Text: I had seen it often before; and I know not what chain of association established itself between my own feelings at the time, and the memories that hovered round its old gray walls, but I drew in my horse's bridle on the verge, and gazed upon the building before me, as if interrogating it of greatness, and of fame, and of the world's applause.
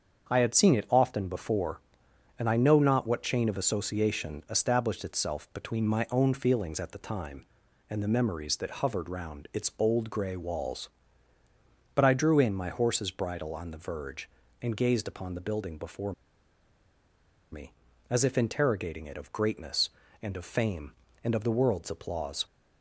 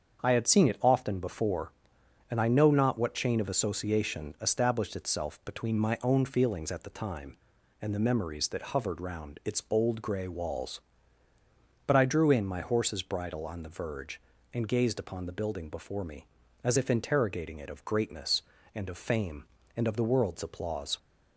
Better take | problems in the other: second | starts louder than the rest; strong; until 1.3 s; 7 dB; strong in the second // pauses between "before" and "me"; strong; at 16.1 s; 1.4 s long

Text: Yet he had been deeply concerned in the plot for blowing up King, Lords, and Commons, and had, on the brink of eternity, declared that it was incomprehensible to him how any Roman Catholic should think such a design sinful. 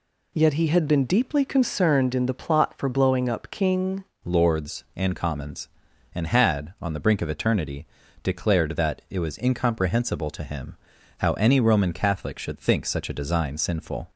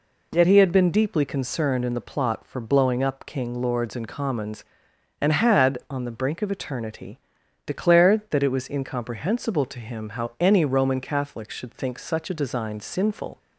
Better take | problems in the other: second | changes voice at "Lords"; from 4.2 s on; 9.8 s long // pauses between "him" and "how"; at 10.7 s; 0.42 s long

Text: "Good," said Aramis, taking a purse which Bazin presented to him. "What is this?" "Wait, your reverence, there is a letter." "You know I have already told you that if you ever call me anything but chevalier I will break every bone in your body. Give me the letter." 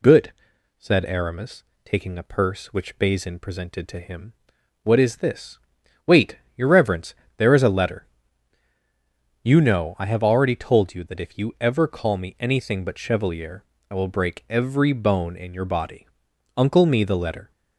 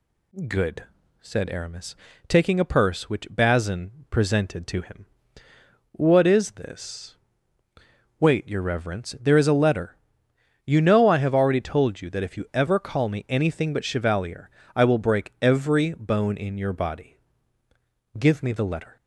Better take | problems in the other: second | pauses between "chevalier" and "I"; slight; at 13.6 s; 0.26 s long; slight in the second // says "Uncle" for "Give"; at 16.5 s

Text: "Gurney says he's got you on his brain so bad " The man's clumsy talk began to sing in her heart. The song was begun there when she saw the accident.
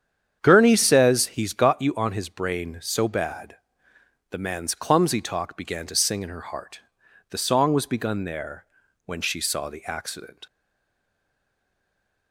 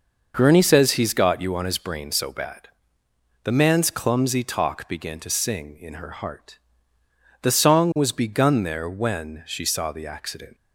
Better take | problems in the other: second | starts louder than the rest; strong; until 1.4 s; 8.5 dB // pauses between "there" and "when"; at 8.6 s; 0.40 s long // stays silent after the last word; noticeable; from 10.4 s on; 1.9 s long

